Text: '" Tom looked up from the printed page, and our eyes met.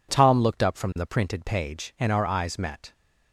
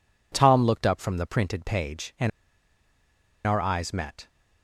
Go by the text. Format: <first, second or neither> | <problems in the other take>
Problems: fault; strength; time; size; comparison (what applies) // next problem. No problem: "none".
first | pauses between "and" and "our"; at 2.3 s; 1.1 s long